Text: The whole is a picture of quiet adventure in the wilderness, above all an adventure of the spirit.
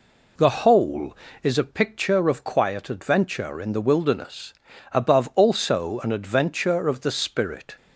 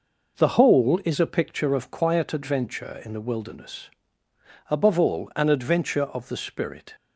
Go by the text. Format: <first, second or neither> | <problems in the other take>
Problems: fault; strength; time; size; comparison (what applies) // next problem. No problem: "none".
second | says "also" for "all"; at 5.3 s